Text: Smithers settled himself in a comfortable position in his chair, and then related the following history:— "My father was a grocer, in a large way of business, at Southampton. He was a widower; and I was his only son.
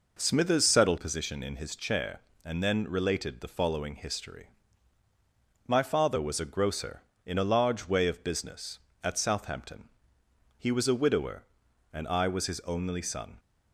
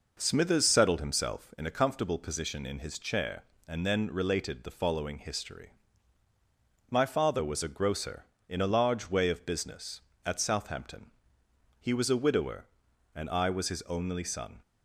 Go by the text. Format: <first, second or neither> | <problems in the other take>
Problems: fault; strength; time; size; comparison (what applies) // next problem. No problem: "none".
second | skips "himself in a comfortable"; at 0.9 s